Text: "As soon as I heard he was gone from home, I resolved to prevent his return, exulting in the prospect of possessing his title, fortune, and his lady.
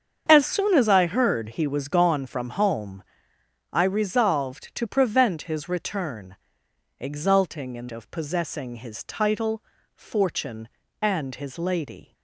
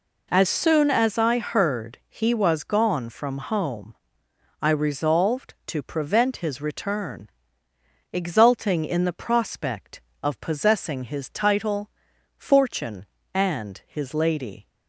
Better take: second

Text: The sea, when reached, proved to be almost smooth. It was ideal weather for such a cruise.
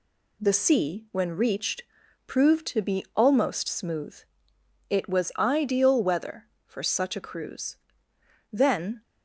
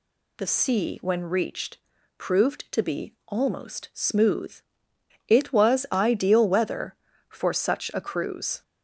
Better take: second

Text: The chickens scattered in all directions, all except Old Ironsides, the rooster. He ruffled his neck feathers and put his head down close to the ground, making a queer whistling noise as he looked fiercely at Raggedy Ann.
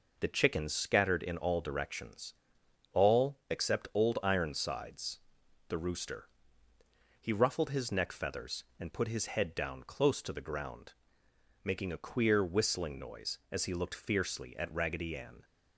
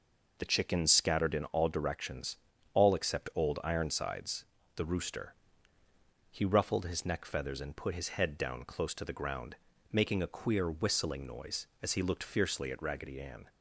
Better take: neither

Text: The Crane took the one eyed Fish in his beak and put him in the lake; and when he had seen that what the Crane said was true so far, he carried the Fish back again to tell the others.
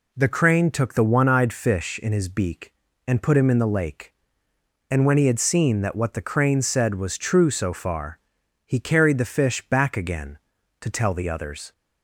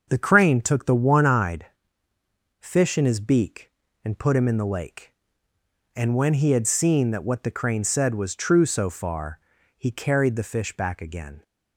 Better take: first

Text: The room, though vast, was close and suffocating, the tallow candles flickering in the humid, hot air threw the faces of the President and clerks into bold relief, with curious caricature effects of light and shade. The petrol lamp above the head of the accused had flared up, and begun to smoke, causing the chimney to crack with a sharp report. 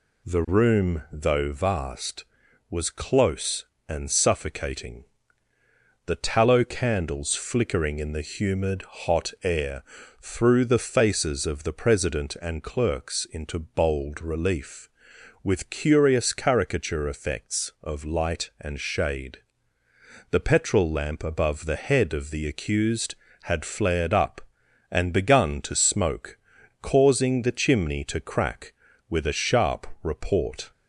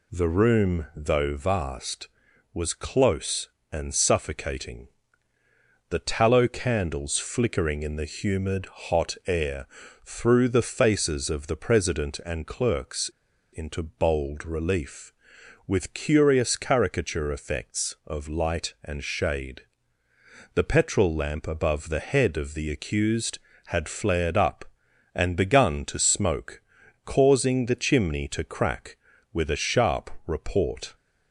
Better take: first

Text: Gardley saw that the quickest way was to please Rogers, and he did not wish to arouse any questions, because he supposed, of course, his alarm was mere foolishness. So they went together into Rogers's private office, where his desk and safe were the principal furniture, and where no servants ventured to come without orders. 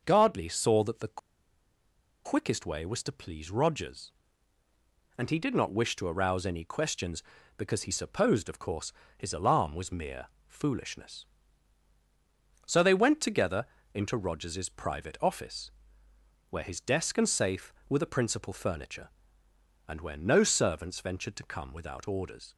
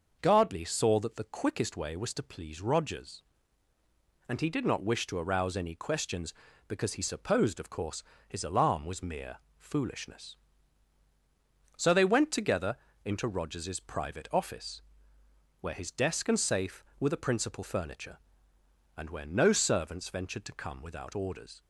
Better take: second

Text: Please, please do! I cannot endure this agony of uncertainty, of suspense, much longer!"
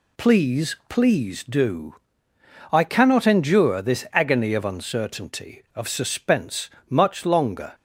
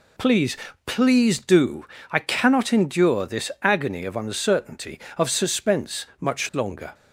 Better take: neither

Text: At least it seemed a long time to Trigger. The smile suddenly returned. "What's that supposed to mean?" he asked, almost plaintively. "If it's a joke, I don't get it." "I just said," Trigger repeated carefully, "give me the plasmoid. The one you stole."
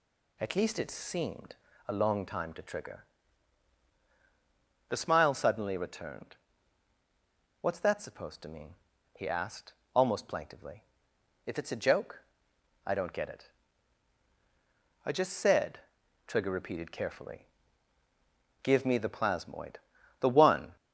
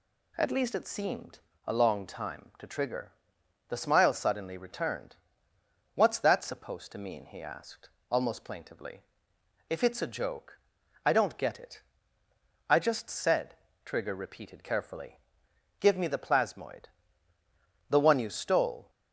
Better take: second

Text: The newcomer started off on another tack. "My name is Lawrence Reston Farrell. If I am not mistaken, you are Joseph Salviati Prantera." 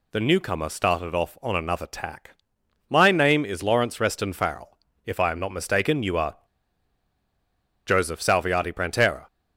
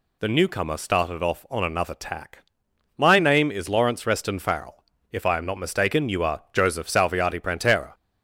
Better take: second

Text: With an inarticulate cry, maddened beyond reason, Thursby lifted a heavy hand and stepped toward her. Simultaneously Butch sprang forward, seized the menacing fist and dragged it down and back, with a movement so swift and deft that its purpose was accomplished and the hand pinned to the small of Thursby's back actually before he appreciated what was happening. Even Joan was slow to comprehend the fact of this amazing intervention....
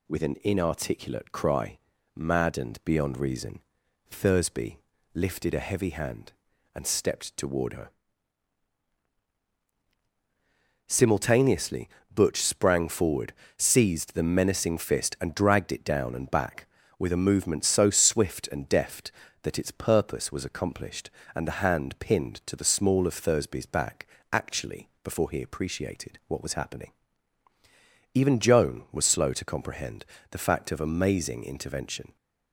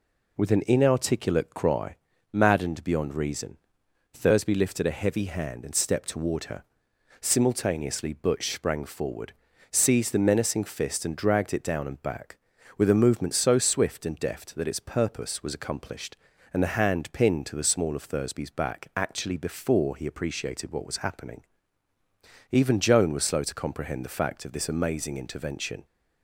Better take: second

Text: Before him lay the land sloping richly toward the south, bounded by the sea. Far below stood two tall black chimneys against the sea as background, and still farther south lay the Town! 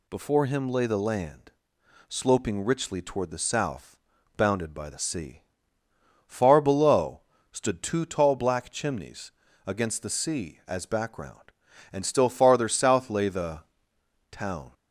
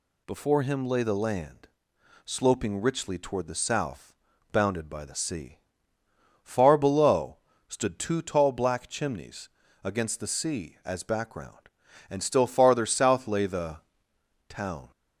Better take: neither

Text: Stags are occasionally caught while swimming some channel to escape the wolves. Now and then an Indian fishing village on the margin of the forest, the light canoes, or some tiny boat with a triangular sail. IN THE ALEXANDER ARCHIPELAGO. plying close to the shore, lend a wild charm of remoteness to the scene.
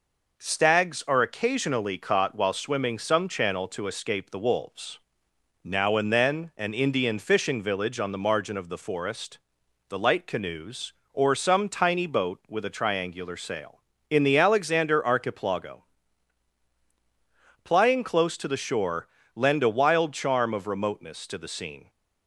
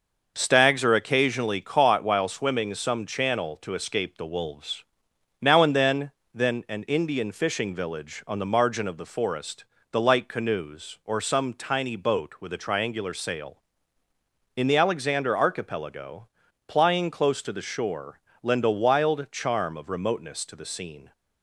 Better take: first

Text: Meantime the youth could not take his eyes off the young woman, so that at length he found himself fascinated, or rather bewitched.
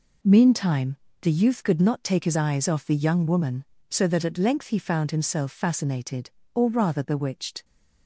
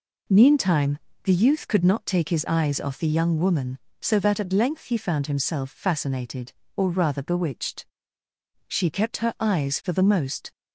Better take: first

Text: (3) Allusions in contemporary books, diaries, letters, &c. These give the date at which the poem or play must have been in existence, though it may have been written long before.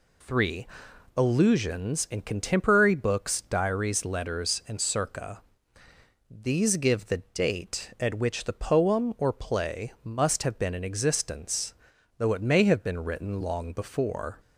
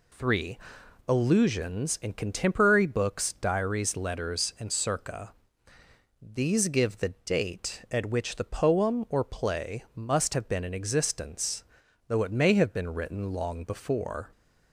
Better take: neither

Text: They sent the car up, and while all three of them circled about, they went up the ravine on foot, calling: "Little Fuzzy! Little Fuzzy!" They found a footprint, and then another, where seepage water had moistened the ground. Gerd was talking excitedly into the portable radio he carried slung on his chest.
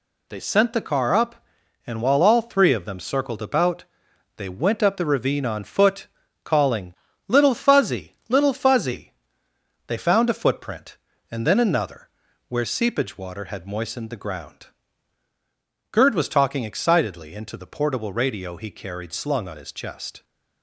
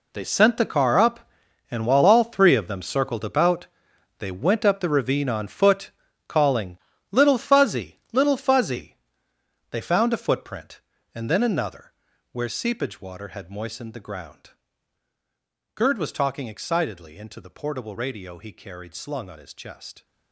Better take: first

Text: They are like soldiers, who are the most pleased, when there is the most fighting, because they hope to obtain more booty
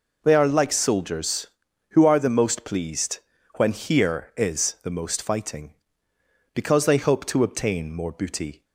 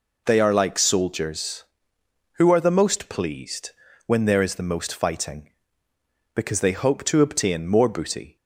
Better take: second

